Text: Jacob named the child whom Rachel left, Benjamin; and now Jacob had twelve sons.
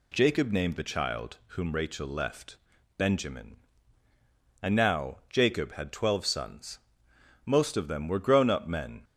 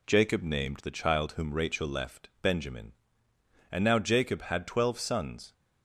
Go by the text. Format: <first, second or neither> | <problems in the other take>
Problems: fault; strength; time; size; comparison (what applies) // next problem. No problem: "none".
second | goes on to say "Most of them were grown up men"; from 7.4 s on; 1.5 s long